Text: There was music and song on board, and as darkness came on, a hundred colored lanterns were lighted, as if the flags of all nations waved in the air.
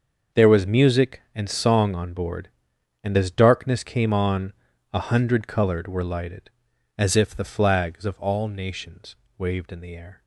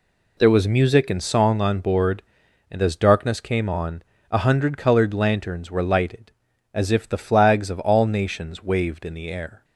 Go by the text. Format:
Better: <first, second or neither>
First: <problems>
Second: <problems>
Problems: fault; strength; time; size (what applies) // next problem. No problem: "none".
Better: second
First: starts louder than the rest; until 1.4 s; 6.5 dB // skips "lanterns"; at 5.8 s // pauses between "nations" and "waved"; slight; at 9.1 s; 0.24 s long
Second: none